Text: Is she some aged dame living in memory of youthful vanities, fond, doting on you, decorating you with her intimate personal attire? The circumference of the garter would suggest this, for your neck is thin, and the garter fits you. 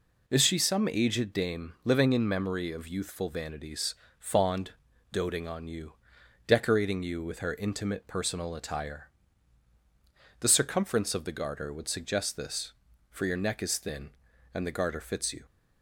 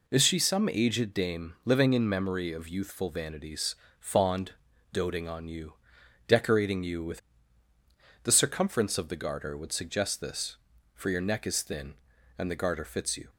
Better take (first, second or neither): first